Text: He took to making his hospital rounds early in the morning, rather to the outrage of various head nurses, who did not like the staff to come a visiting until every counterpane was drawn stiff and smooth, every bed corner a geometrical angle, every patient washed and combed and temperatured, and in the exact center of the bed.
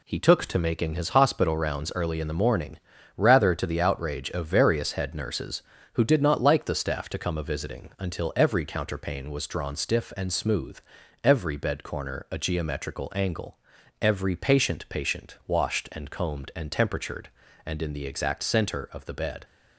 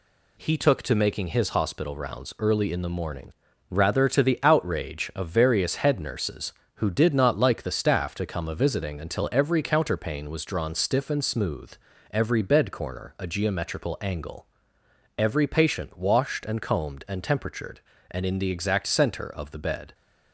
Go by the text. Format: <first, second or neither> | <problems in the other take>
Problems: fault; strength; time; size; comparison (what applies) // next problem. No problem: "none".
second | says "patient" twice; at 14.8 s